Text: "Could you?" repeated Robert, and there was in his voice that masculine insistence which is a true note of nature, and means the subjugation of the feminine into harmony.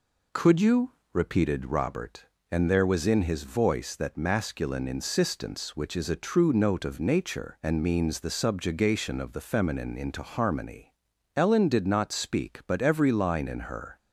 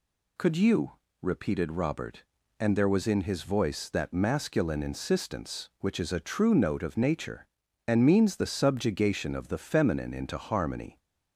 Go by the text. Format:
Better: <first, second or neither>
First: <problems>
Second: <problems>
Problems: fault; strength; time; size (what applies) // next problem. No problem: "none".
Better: second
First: goes on to say "Ellen did not speak but every line in her"; strong; from 11.3 s on; 2.6 s long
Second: none